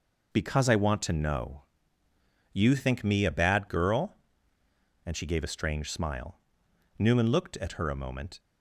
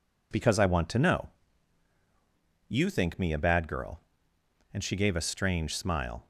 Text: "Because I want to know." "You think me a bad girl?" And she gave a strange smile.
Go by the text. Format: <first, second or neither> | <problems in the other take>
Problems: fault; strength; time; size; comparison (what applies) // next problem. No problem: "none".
second | goes on to say "Newman looked at her a moment"; from 6.9 s on; 1.4 s long